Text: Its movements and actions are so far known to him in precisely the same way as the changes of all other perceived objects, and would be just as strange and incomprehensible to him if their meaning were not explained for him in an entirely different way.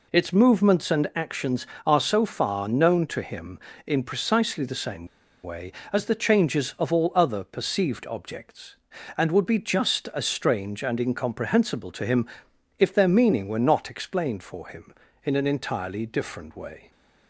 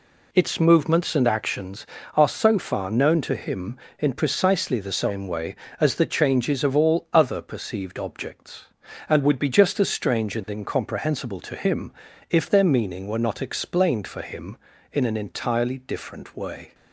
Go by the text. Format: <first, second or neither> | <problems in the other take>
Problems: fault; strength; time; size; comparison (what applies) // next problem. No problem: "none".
second | pauses between "same" and "way"; at 5.0 s; 0.37 s long // pauses between "him" and "if"; noticeable; at 12.2 s; 0.52 s long; also in the second